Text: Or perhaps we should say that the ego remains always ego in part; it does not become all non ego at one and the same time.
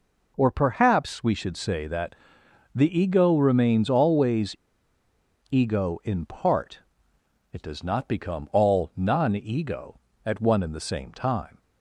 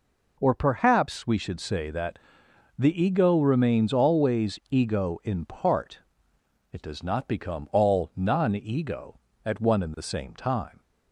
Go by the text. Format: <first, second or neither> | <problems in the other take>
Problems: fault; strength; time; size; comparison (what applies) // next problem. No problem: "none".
second | pauses between "that" and "the"; noticeable; at 2.1 s; 0.60 s long; noticeable in the second // pauses between "always" and "ego"; noticeable; at 4.5 s; 0.93 s long